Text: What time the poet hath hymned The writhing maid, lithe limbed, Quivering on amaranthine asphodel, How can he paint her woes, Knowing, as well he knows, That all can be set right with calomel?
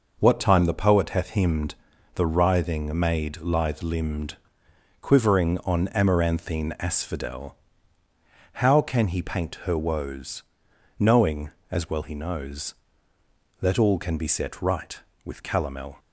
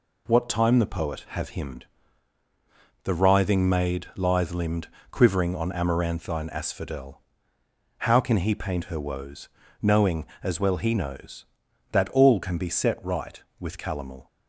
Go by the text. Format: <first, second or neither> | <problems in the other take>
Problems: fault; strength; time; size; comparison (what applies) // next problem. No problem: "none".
first | says "have" for "hath"; at 1.2 s // pauses between "hymned" and "The"; at 1.8 s; 1.2 s long; also in the first